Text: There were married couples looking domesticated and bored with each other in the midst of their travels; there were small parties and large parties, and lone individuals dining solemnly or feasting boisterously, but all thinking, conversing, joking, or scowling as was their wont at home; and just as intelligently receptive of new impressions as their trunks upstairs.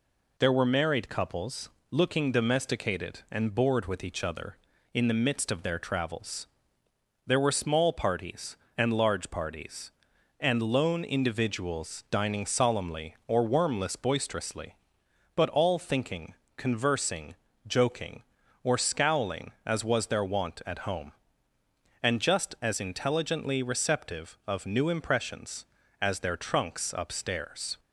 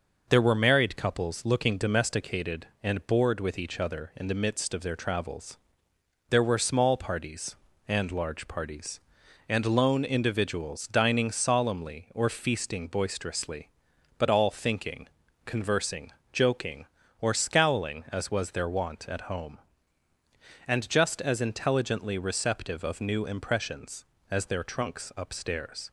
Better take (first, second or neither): second